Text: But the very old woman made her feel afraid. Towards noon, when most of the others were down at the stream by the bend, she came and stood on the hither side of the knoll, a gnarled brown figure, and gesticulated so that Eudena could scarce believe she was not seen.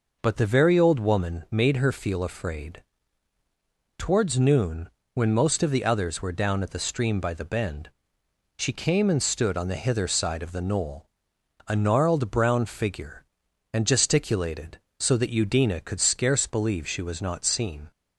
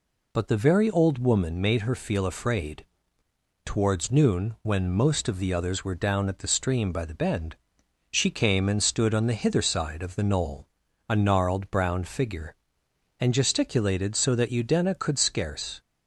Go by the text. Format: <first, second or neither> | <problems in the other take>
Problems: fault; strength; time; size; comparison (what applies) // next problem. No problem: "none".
first | stops before "believe she was not seen"; at 15.8 s